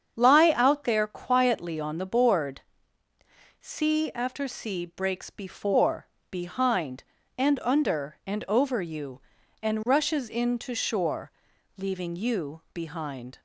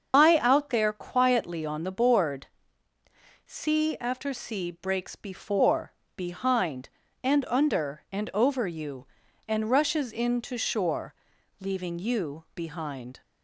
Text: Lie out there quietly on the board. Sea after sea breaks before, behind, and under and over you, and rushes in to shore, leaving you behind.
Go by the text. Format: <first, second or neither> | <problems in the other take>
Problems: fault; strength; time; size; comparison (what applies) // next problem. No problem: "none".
first | loses the start of "Lie"; at 0.1 s; 115 ms // starts louder than the rest; until 1.1 s; 6.5 dB; strong in the first